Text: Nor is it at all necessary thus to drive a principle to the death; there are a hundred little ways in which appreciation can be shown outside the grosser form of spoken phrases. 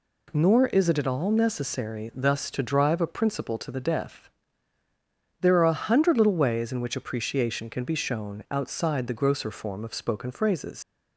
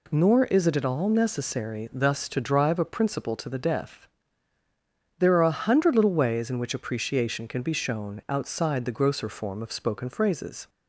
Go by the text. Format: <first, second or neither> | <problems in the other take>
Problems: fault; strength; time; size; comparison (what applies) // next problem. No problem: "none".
second | leaves "phrases" unfinished; at 10.8 s; 80 ms